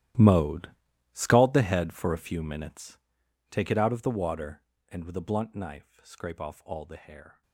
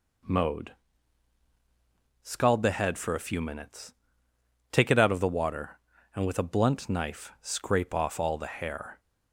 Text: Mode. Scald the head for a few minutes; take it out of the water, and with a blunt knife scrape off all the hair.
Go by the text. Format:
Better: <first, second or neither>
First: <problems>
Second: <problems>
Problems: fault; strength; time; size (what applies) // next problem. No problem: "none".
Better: second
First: gets quieter; strong; throughout; 18.5 dB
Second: none